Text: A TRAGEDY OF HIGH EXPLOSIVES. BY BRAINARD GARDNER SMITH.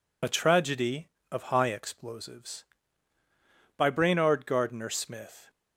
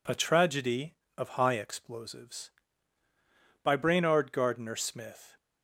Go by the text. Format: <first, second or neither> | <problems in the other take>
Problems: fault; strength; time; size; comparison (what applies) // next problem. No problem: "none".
second | loses the start of "A"; at 0.2 s; 35 ms